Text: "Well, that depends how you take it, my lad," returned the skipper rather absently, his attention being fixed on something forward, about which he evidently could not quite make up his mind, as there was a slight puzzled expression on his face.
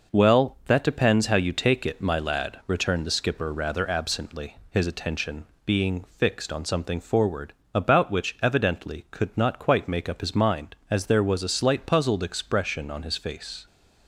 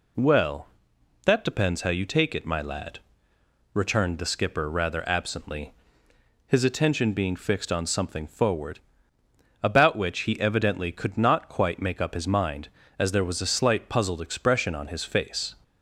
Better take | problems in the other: second | pauses between "attention" and "being"; slight; at 5.4 s; 0.22 s long // skips "he"; at 8.3 s

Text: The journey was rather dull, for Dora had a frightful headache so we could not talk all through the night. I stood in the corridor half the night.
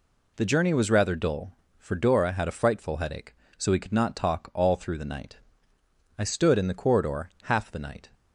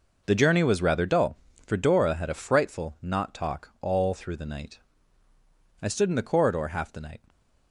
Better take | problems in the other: first | skips "headache so we could"; at 2.9 s

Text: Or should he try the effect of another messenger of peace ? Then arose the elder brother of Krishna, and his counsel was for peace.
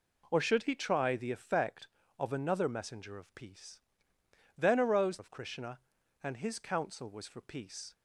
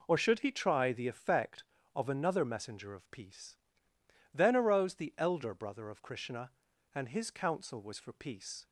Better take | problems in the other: second | skips "the elder brother"; at 5.1 s

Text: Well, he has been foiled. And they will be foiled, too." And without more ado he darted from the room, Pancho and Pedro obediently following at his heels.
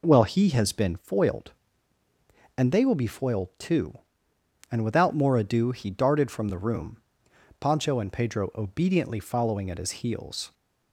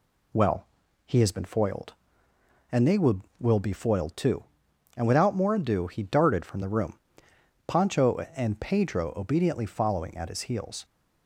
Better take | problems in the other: first | says "will" twice; at 3.3 s

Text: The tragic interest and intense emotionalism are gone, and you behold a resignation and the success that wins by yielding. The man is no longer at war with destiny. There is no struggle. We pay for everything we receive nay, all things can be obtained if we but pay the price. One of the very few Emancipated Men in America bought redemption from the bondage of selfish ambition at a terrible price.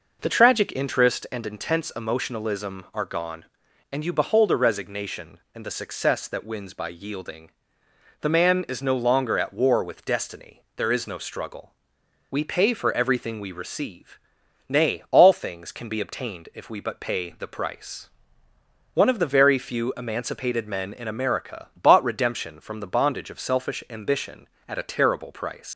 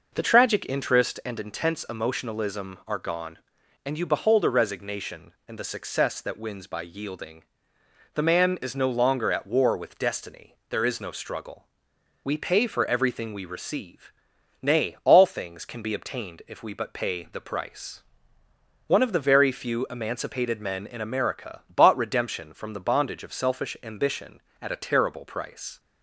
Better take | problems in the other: second | pauses between "receive" and "nay"; noticeable; at 14.1 s; 0.50 s long; noticeable in the second // leaves "price" unfinished; at 25.7 s; 130 ms

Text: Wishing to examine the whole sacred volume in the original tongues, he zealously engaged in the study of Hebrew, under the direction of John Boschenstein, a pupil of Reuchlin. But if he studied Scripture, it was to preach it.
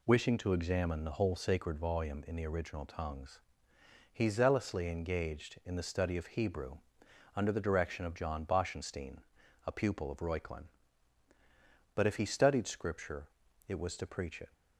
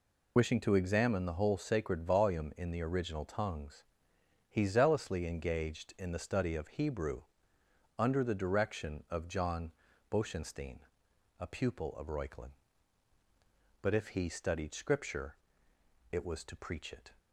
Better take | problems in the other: first | loses the start of "Wishing"; at 0.3 s; 30 ms // pauses between "John" and "Boschenstein"; slight; at 9.7 s; 0.36 s long

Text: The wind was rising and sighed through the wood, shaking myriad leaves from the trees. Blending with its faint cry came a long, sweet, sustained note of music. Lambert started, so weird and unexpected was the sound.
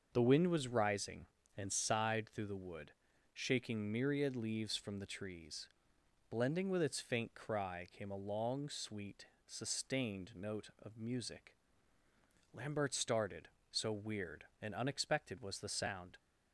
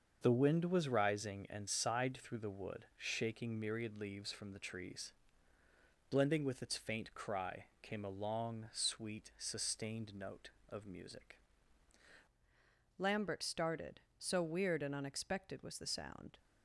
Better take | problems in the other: first | starts louder than the rest; until 1.2 s; 6.5 dB; also in the first // pauses between "cry" and "came"; slight; at 7.6 s; 0.18 s long // changes voice at "Lambert"; from 12.9 s on; 3.4 s long

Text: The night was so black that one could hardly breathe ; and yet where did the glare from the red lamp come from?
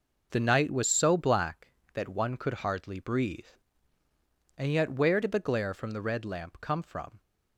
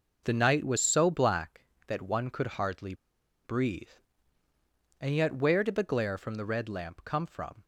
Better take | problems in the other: first | pauses between "hardly" and "breathe"; noticeable; at 2.9 s; 0.51 s long

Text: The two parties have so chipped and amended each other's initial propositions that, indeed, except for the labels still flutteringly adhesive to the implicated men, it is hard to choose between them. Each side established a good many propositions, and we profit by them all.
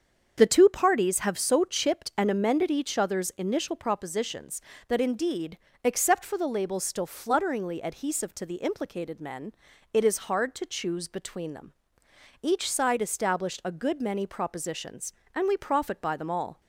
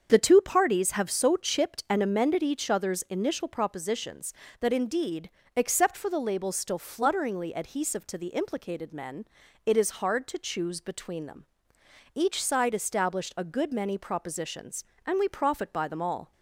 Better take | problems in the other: neither | starts louder than the rest; the same in both

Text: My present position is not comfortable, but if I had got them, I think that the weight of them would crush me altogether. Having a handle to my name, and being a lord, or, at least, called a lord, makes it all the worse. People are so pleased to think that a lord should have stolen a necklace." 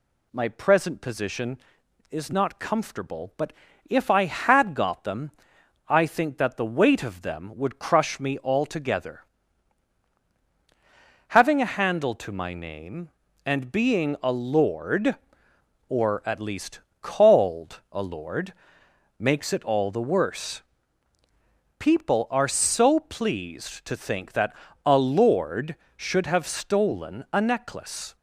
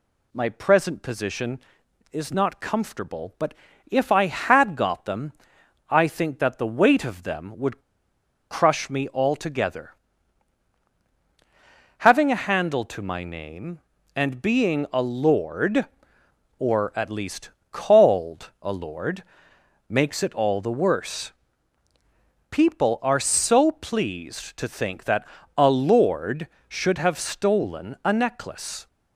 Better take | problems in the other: first | pauses between "but" and "if"; at 3.5 s; 0.38 s long; also in the first // pauses between "would" and "crush"; noticeable; at 7.8 s; 0.69 s long // pauses between "that" and "a"; slight; at 25.2 s; 0.32 s long; slight in the first

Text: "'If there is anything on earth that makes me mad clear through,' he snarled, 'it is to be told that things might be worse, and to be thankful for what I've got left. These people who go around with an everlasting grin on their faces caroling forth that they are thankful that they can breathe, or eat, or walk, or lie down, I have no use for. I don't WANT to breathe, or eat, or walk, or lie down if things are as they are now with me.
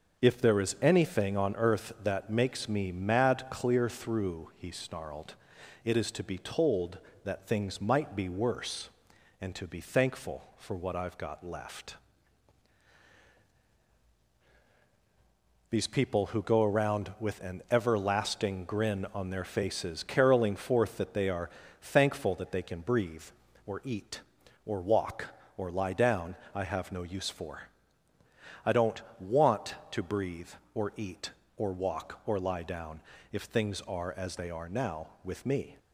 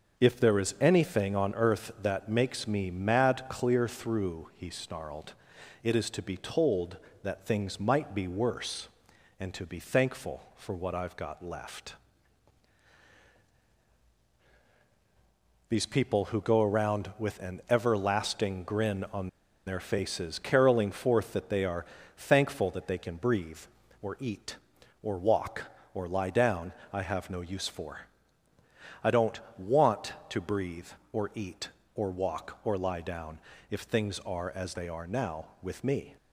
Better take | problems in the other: first | starts louder than the rest; until 1.2 s; 7 dB; also in the first // pauses between "on" and "their"; at 19.2 s; 0.38 s long // pauses between "are" and "thankful"; slight; at 21.8 s; 0.30 s long; slight in the first // pauses between "don't" and "WANT"; slight; at 29.3 s; 0.18 s long; slight in the first // pauses between "down" and "if"; slight; at 33.3 s; 0.32 s long; slight in the first

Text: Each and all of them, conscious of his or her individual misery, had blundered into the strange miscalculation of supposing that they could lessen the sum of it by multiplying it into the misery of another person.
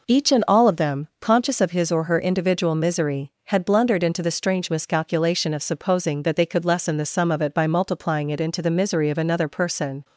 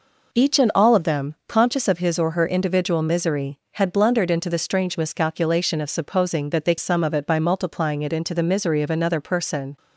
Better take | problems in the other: first | skips "could lessen the"; at 6.7 s

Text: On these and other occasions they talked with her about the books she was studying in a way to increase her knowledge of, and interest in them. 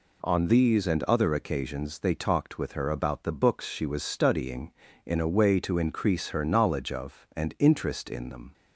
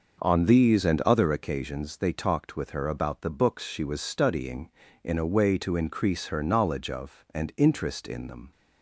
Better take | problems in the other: first | starts louder than the rest; noticeable; until 1.4 s; 6 dB

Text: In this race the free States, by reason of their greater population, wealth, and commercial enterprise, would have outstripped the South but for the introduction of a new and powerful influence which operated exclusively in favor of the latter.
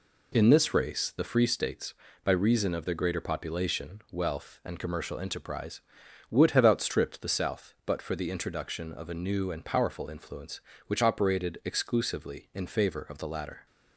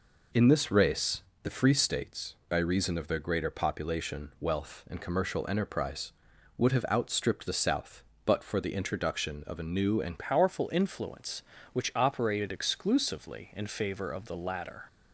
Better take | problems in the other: first | pauses between "race" and "the"; slight; at 1.2 s; 0.22 s long // changes voice at "powerful"; from 10.1 s on; 4.7 s long

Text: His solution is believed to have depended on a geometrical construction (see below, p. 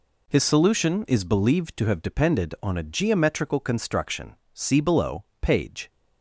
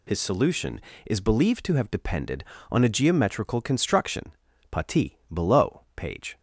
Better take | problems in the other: first | says "pati" for "see"; at 4.6 s

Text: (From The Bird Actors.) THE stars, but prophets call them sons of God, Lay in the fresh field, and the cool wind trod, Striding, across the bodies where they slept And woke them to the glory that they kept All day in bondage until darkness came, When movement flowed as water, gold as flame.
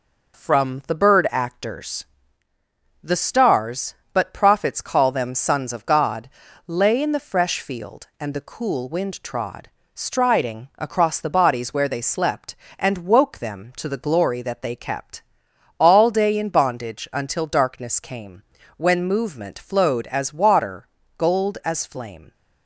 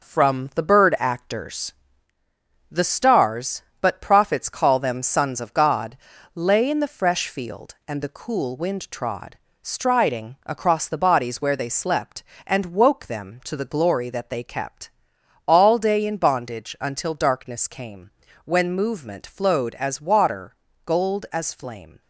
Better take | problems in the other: first | gets quieter; noticeable; throughout; 4.5 dB // pauses between "kept" and "All"; noticeable; at 14.9 s; 0.56 s long; noticeable in the first

